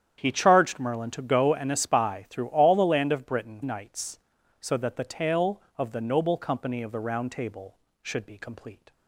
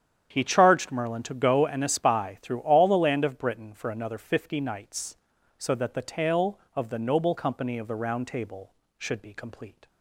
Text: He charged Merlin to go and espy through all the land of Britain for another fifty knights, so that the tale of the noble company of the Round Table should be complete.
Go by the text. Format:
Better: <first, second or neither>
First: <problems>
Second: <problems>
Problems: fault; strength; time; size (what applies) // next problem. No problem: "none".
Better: second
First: starts louder than the rest; strong; until 1.1 s; 9.5 dB // skips "for another fifty"; at 3.6 s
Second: starts louder than the rest; strong; until 1.3 s; 9 dB